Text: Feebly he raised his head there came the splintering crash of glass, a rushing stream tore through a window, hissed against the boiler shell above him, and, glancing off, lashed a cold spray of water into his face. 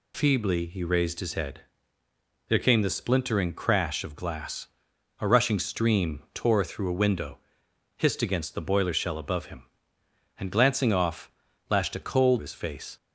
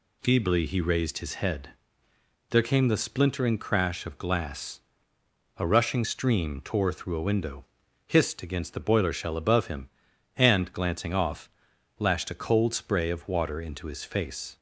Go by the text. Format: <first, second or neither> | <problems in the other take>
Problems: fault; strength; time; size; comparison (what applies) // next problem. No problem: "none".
second | pauses between "head" and "there"; noticeable; at 1.5 s; 0.88 s long; noticeable in the second // skips "spray of water into"; at 12.3 s